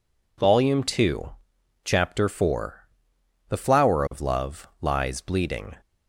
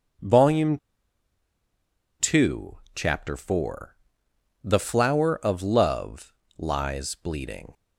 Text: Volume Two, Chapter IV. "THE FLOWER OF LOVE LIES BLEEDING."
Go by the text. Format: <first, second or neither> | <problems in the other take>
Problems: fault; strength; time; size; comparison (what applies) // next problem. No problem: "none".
first | starts louder than the rest; until 2.6 s; 6 dB // pauses between "Volume" and "Two"; strong; at 0.7 s; 1.4 s long // pauses between "LOVE" and "LIES"; slight; at 6.3 s; 0.24 s long